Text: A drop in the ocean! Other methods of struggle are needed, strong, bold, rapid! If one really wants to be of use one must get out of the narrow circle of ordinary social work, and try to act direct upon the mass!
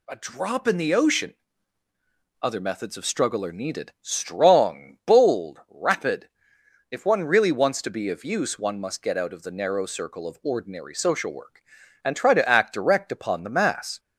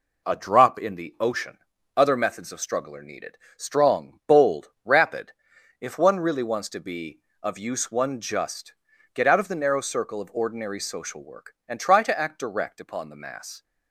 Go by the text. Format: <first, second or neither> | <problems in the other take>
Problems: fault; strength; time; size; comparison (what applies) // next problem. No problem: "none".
first | says "just" for "must"; at 8.2 s